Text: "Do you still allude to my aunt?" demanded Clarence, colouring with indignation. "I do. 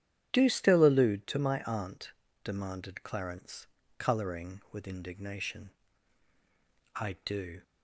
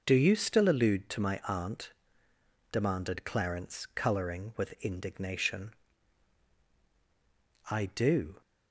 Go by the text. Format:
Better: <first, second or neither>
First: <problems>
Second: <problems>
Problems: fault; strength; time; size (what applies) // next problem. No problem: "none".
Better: second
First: starts louder than the rest; strong; until 1.3 s; 10 dB // skips "you"; at 0.4 s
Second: none